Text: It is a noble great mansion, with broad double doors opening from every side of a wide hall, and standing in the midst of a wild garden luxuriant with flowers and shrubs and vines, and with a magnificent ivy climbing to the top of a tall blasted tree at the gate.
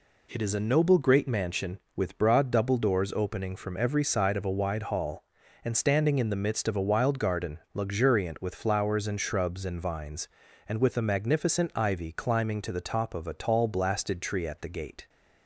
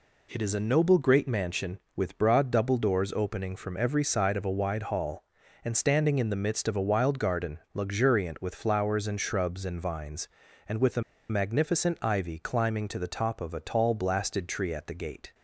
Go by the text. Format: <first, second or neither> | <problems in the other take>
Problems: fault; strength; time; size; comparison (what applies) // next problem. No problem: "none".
first | pauses between "garden" and "luxuriant"; slight; at 7.5 s; 0.16 s long; slight in the first // pauses between "a" and "magnificent"; slight; at 11.0 s; 0.28 s long